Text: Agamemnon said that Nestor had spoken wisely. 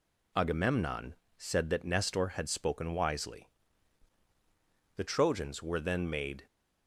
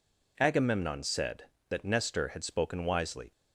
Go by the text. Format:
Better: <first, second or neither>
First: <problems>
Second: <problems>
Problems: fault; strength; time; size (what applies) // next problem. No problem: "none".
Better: second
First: pauses between "Agamemnon" and "said"; slight; at 1.1 s; 0.22 s long // goes on to say "The Trojans were then made"; from 4.9 s on; 1.4 s long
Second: none